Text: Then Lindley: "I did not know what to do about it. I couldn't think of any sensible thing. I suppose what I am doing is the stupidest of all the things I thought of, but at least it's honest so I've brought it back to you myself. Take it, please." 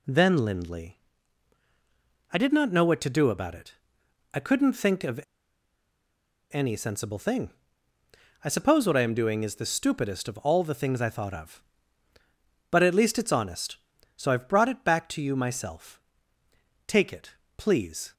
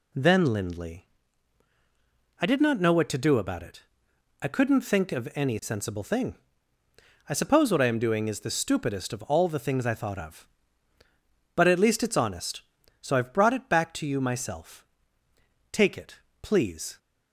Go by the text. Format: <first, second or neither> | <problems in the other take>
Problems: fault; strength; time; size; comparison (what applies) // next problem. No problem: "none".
second | pauses between "of" and "any"; strong; at 5.1 s; 1.3 s long